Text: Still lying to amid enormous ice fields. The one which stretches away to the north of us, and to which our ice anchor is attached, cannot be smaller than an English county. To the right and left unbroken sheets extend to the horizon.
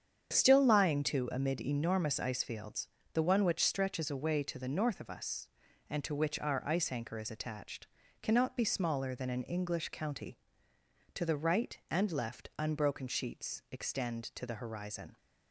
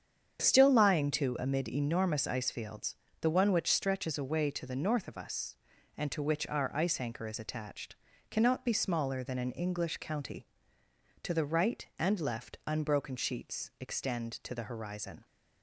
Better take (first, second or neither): neither